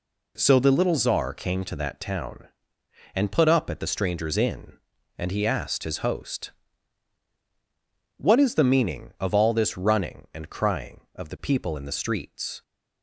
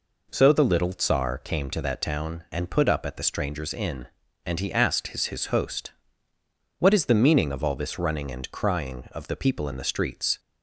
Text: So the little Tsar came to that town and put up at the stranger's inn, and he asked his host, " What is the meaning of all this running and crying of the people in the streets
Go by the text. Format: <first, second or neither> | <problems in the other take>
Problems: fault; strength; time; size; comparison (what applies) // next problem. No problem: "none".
first | says "his" twice; at 5.2 s